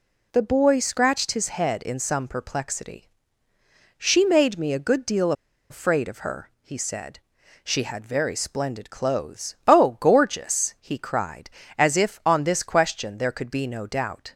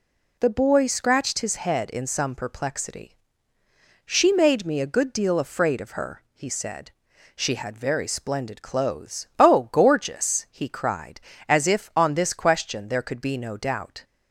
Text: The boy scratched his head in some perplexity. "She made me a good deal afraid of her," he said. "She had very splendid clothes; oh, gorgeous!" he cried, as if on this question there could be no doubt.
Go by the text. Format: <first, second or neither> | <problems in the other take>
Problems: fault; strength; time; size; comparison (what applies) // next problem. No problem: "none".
second | pauses between "deal" and "afraid"; at 5.3 s; 0.37 s long